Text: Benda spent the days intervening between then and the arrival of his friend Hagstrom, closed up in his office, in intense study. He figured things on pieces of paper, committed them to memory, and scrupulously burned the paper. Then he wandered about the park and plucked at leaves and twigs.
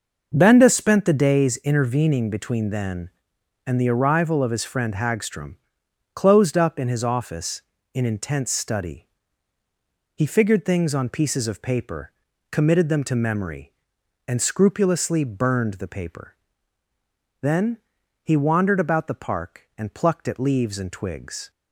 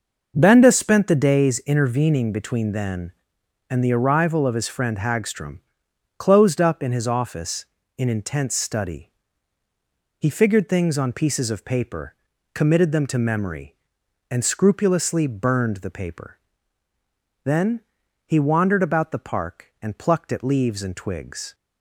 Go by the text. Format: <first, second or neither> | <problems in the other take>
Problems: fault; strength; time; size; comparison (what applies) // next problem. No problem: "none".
neither | pauses between "Then" and "he"; the same in both